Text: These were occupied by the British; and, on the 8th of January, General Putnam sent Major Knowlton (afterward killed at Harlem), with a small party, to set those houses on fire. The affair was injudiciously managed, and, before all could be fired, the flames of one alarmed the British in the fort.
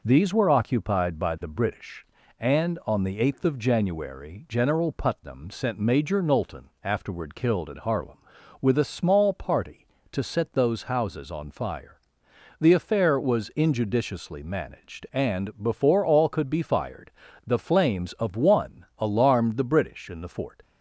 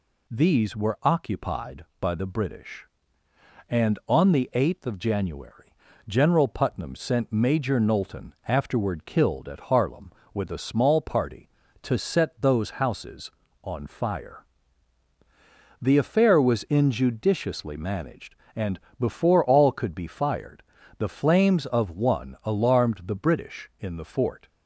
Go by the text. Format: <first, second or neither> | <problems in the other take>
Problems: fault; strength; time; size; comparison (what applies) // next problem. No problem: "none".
neither | none